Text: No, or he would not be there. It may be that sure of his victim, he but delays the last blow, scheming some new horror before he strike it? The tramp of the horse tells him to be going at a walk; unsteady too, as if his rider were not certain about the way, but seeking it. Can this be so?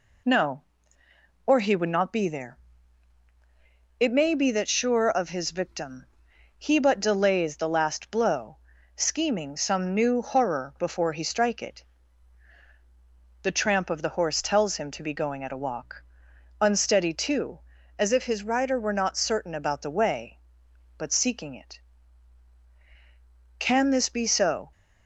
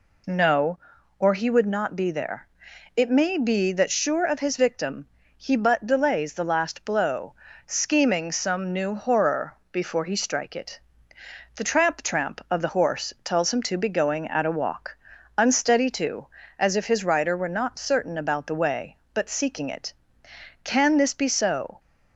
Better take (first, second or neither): first